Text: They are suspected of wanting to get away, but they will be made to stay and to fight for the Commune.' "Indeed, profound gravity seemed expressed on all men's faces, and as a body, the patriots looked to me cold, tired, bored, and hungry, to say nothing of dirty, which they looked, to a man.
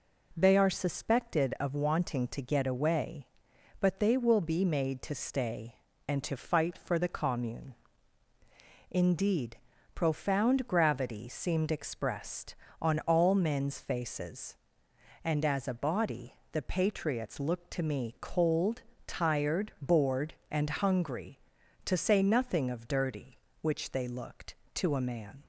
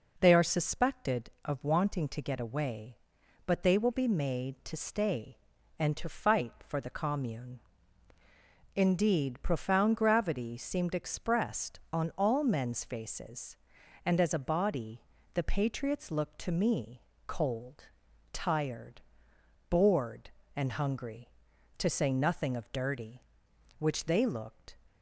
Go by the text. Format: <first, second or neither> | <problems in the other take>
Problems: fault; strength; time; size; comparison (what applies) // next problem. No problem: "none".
first | pauses between "me" and "cold"; slight; at 17.0 s; 0.24 s long // stops before "to a man"; at 24.8 s